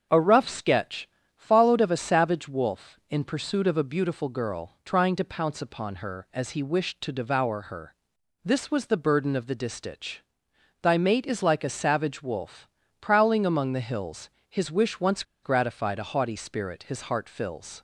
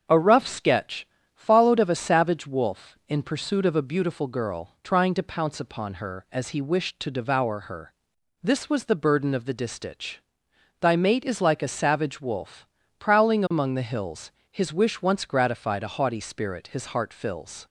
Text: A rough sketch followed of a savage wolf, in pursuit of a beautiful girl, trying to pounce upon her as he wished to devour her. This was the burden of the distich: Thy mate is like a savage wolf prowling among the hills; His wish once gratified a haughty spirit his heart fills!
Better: second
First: starts louder than the rest; strong; until 1.3 s; 7.5 dB // pauses between "sketch" and "followed"; slight; at 1.0 s; 0.28 s long // pauses between "wolf" and "prowling"; slight; at 12.6 s; 0.32 s long // pauses between "once" and "gratified"; slight; at 15.2 s; 0.20 s long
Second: starts louder than the rest; strong; until 1.3 s; 7.5 dB // pauses between "sketch" and "followed"; slight; at 1.0 s; 0.28 s long // pauses between "wolf" and "prowling"; slight; at 12.6 s; 0.32 s long

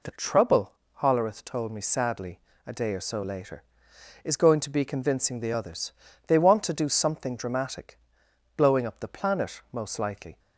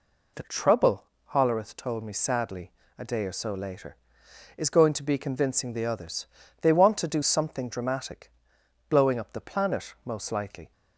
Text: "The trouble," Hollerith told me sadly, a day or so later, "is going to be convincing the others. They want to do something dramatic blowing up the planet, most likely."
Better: neither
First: pauses between "dramatic" and "blowing"; noticeable; at 7.9 s; 0.58 s long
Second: pauses between "dramatic" and "blowing"; noticeable; at 8.3 s; 0.58 s long

